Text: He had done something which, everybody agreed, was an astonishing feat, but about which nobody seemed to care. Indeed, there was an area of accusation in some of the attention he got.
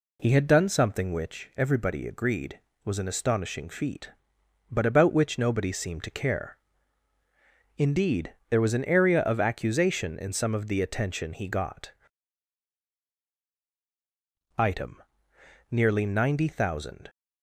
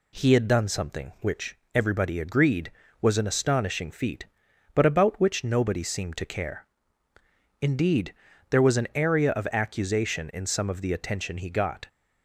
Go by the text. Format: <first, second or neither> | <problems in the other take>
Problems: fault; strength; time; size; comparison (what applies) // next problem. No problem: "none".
second | goes on to say "Item nearly ninety thousand"; strong; from 14.5 s on; 2.5 s long